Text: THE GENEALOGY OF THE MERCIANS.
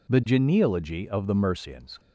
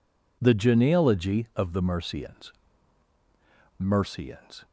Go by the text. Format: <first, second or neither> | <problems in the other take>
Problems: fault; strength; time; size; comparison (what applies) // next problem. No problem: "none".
first | says "MERCIANS" twice; at 3.7 s